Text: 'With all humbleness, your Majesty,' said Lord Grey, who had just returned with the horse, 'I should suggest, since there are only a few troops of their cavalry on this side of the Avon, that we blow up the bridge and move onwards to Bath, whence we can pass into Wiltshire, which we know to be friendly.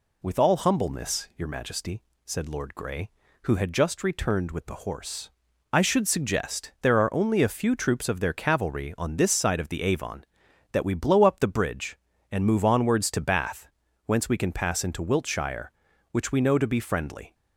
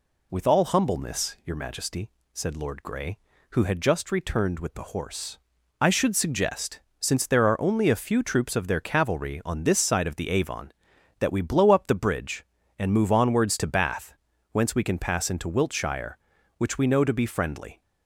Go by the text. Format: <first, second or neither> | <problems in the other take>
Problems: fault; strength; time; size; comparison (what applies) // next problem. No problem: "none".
second | skips "since"; at 6.7 s